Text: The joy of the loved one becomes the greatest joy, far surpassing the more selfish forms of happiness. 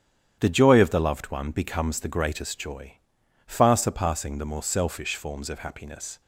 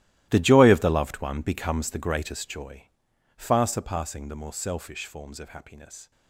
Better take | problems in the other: first | gets quieter; strong; throughout; 17.5 dB // starts louder than the rest; strong; until 1.3 s; 15.5 dB; strong in the first

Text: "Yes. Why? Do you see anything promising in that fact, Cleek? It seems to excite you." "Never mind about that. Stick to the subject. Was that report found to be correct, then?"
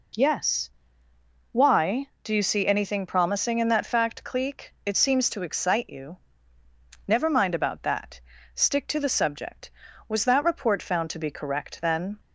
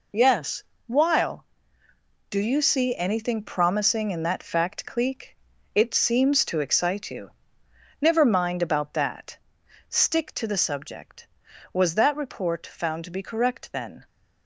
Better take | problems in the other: first | says "While" for "Why"; at 0.8 s

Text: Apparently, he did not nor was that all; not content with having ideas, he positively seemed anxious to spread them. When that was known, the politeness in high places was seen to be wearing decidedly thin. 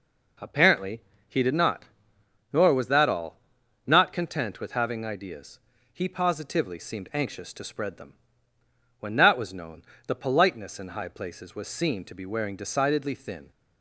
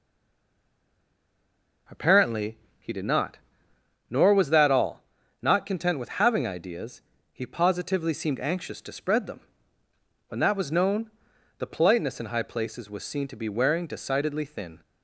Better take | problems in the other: first | stays silent before the first word; noticeable; until 1.8 s; 1.8 s long // pauses between "not" and "nor"; noticeable; at 3.3 s; 0.72 s long; noticeable in the first

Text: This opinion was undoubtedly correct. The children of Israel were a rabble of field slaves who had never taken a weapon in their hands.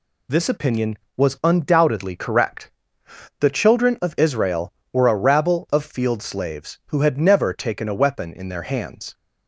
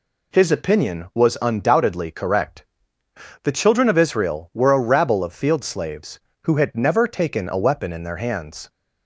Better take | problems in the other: first | says "His" for "This"; at 0.3 s

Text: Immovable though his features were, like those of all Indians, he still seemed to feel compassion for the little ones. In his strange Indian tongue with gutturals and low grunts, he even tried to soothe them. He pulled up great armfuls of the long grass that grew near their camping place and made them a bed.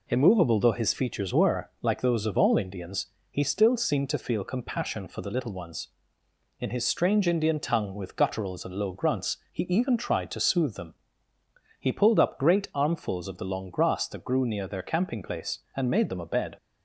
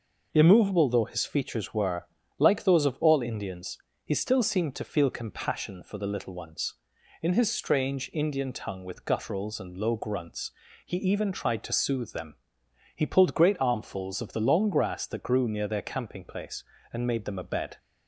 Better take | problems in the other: first | skips "up"; at 13.3 s

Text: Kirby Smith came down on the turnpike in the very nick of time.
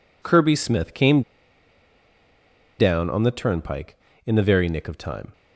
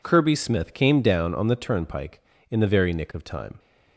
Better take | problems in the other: second | pauses between "came" and "down"; strong; at 1.2 s; 1.5 s long

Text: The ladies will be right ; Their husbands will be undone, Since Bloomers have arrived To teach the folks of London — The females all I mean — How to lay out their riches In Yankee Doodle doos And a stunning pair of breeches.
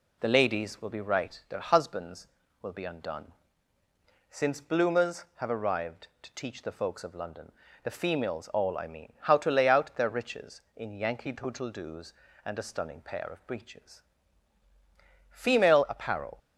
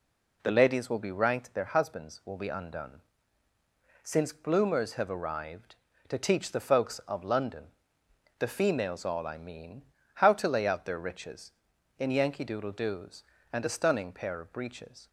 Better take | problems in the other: second | goes on to say "Female apparel"; noticeable; from 15.3 s on; 1.0 s long

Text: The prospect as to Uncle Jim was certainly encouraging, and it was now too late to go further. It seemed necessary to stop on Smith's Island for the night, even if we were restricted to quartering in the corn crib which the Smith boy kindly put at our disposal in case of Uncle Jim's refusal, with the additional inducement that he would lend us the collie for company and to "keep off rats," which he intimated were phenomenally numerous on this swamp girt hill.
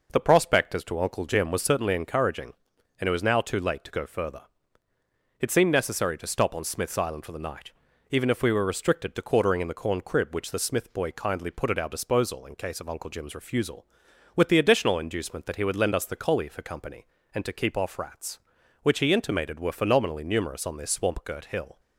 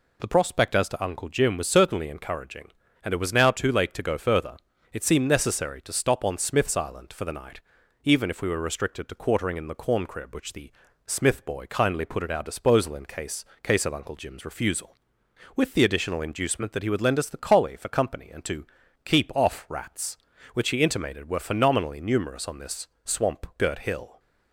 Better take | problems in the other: first | pauses between "the" and "Smith"; slight; at 10.7 s; 0.36 s long // says "case" twice; at 13.6 s // pauses between "to" and "keep"; at 18.6 s; 0.38 s long // pauses between "this" and "swamp"; slight; at 22.8 s; 0.16 s long

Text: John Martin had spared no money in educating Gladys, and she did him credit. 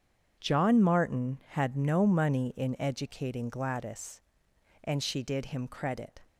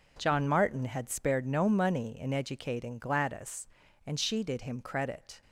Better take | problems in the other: second | starts louder than the rest; strong; until 1.4 s; 7.5 dB // skips "spared"; at 1.7 s

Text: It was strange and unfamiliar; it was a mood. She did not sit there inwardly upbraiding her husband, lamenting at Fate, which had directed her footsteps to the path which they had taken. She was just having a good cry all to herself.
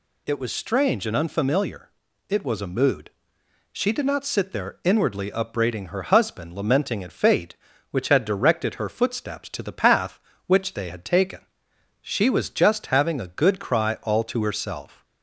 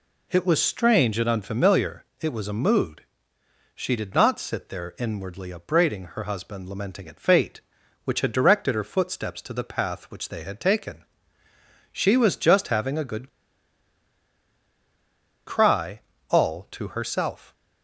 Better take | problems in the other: first | pauses between "good" and "cry"; strong; at 13.2 s; 2.1 s long // pauses between "cry" and "all"; slight; at 16.0 s; 0.28 s long

